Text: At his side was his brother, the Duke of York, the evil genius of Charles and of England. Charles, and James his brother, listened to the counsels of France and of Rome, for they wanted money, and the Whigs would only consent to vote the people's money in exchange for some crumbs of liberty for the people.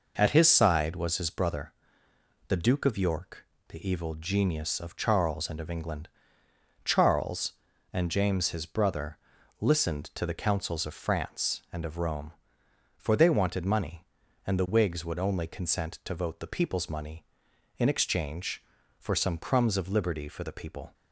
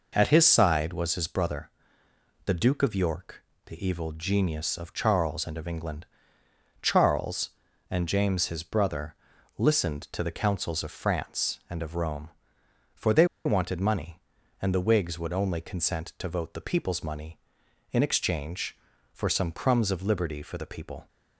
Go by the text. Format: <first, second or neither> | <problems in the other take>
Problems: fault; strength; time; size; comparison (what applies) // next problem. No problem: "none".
first | pauses between "they" and "wanted"; slight; at 13.2 s; 0.19 s long